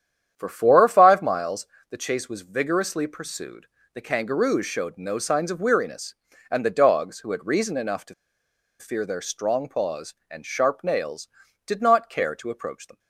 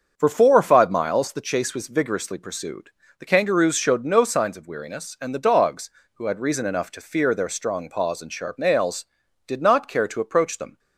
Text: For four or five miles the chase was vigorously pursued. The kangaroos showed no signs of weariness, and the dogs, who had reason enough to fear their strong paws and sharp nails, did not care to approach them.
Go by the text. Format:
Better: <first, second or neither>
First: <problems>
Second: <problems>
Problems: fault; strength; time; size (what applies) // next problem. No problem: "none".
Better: second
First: starts louder than the rest; strong; until 1.3 s; 9.5 dB // pauses between "miles" and "the"; slight; at 1.6 s; 0.26 s long // pauses between "to" and "fear"; noticeable; at 8.1 s; 0.66 s long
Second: starts louder than the rest; until 1.1 s; 6.5 dB